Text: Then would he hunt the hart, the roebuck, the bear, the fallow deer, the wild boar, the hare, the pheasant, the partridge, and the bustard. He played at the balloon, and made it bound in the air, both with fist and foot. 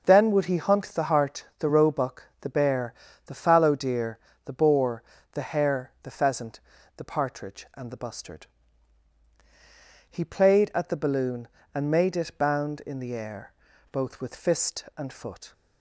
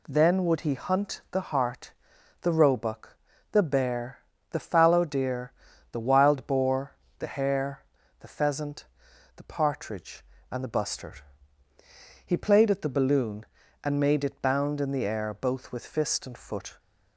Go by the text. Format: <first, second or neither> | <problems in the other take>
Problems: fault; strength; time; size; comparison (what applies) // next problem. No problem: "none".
second | skips "wild"; at 4.5 s